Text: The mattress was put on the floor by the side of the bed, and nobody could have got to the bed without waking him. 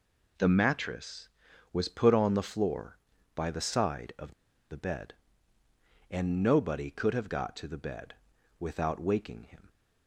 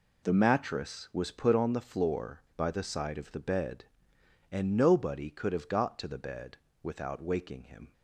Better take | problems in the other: second | pauses between "of" and "the"; at 4.3 s; 0.37 s long // pauses between "bed" and "without"; at 8.1 s; 0.44 s long; slight in the second

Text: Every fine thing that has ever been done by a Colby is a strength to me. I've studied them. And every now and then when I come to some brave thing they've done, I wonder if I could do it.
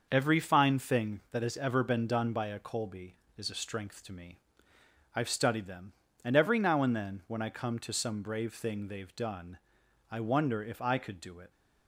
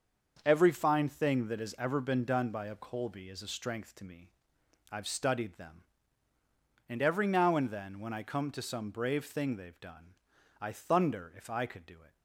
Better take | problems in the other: first | starts louder than the rest; until 1.4 s; 6.5 dB; noticeable in the first // says "thunder" for "wonder"; at 10.7 s

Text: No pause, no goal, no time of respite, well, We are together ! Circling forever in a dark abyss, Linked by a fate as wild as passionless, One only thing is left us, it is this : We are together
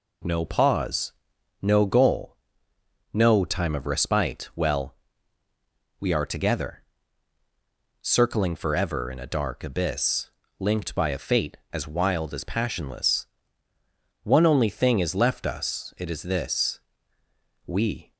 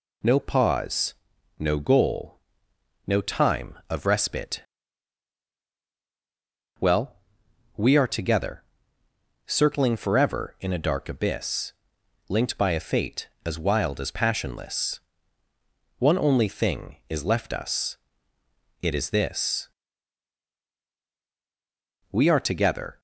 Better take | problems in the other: second | stops before "are together"; at 18.1 s

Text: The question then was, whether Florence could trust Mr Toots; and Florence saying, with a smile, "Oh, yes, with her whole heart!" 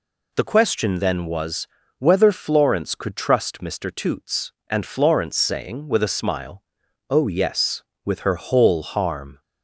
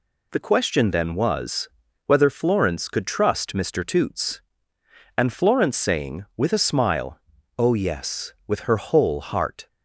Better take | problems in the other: second | says "harm" for "heart"; at 8.8 s

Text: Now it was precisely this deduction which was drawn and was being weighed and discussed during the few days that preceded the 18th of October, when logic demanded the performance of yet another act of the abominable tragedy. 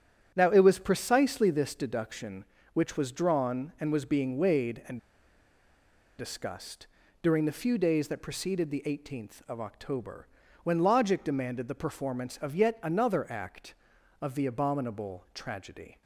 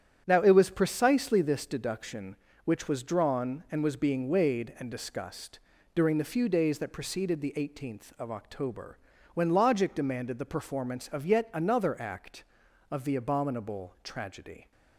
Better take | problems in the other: second | starts louder than the rest; strong; until 1.3 s; 9.5 dB; strong in the second // pauses between "and" and "discussed"; at 4.9 s; 1.2 s long // pauses between "discussed" and "during"; slight; at 6.8 s; 0.34 s long; slight in the second

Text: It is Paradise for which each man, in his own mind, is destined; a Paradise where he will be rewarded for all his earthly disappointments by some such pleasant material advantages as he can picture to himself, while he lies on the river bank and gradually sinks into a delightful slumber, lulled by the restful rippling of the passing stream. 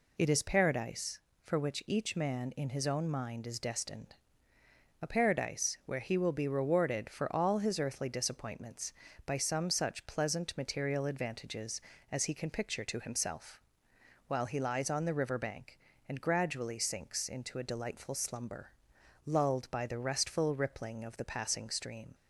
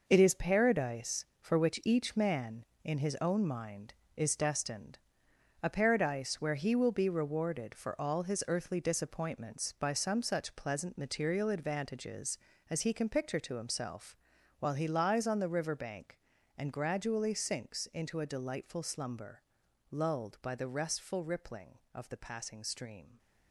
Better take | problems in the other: first | gets quieter; strong; throughout; 9 dB

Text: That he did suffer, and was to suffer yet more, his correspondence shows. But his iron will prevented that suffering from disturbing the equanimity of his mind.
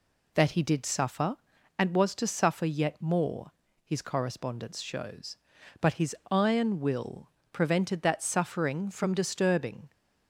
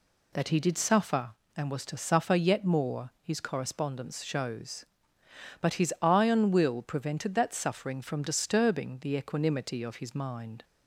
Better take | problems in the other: second | pauses between "his" and "iron"; slight; at 6.1 s; 0.16 s long // pauses between "will" and "prevented"; slight; at 7.2 s; 0.22 s long // stops before "the equanimity of his mind"; at 9.9 s

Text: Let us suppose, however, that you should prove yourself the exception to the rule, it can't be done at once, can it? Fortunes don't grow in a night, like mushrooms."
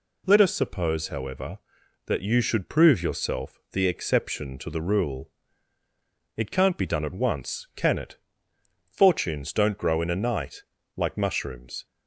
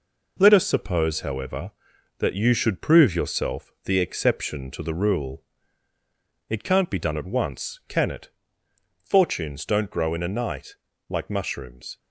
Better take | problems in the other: first | gets quieter; throughout; 6.5 dB

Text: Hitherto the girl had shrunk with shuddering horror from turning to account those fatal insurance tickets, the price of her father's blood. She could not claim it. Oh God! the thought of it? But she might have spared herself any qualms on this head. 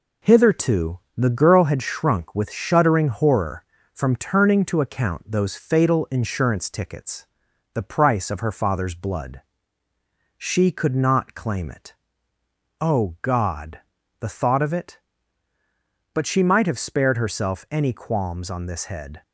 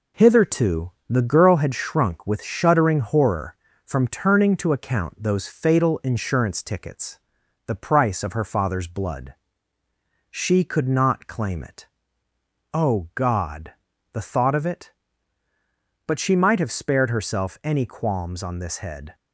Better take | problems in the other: neither | pauses between "Hitherto" and "the"; slight; the same in both

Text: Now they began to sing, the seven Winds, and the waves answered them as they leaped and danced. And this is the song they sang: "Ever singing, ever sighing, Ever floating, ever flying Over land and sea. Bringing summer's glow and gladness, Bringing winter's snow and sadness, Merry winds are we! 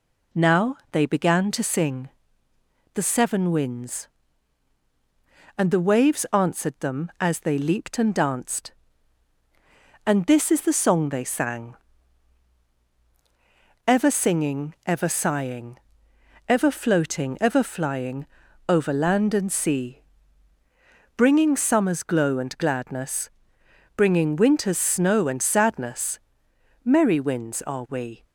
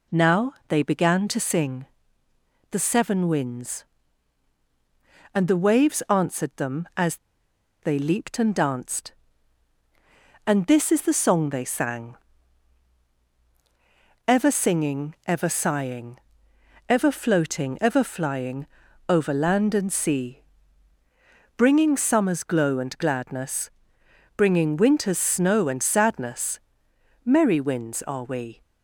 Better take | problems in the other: first | pauses between "as" and "they"; noticeable; at 7.1 s; 0.66 s long // pauses between "flying" and "Over"; at 18.6 s; 0.42 s long; also in the first

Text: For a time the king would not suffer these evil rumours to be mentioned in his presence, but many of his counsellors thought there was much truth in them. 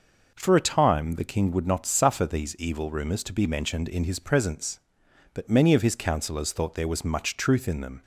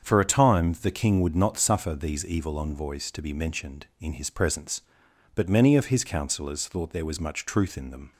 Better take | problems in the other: first | starts louder than the rest; strong; until 1.1 s; 7.5 dB // says "envoys" for "rumours"; at 2.5 s

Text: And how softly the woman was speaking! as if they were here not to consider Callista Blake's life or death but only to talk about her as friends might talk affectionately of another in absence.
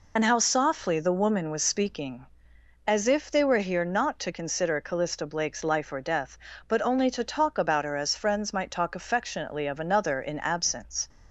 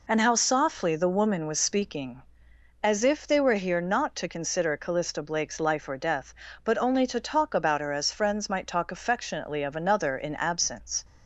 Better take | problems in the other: second | loses the start of "And"; at 0.1 s; 30 ms

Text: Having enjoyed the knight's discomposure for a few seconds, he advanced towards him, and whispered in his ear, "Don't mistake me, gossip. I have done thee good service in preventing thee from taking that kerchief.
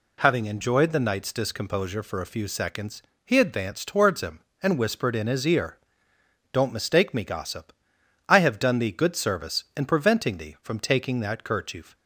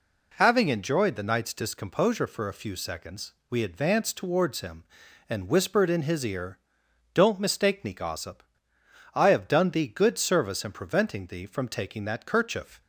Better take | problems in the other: first | says "we" for "he"; at 3.5 s

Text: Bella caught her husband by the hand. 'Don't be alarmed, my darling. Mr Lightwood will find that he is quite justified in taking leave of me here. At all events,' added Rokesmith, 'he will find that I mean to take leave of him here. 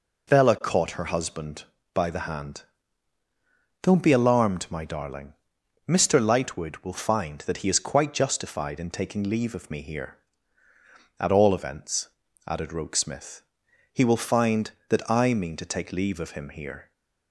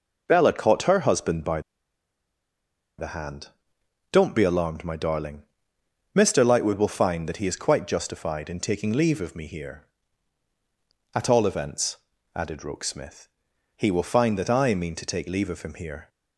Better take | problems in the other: first | pauses between "by" and "the"; strong; at 1.6 s; 1.3 s long

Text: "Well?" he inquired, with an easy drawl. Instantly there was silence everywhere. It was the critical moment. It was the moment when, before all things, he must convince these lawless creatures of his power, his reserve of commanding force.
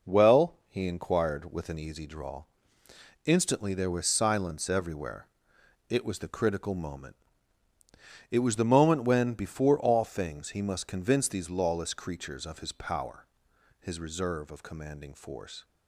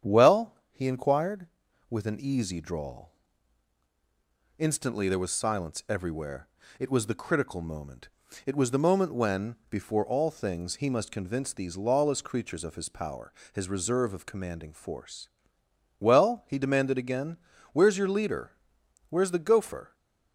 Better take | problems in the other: first | starts louder than the rest; strong; until 1.2 s; 8.5 dB // goes on to say "Well he demanded again Where's your leader Where's the gopher"; strong; from 15.9 s on; 3.9 s long

